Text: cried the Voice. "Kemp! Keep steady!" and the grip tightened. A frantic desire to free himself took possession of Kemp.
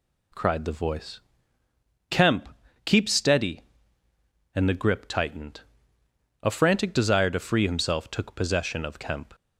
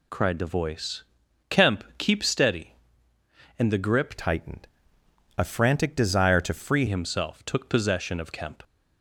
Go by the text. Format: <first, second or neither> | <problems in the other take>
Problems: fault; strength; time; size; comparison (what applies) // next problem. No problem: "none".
first | changes voice from "tightened" to "free"; from 4.1 to 6.8 s; 2.7 s long